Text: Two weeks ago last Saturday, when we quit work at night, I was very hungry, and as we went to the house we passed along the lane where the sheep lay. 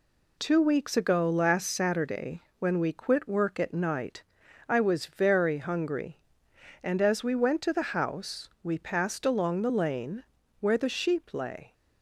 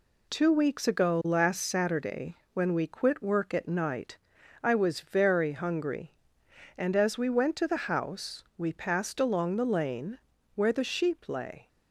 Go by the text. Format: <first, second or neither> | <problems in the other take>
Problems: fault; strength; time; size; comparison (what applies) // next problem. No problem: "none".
neither | pauses between "house" and "we"; slight; the same in both // pauses between "lane" and "where"; slight; the same in both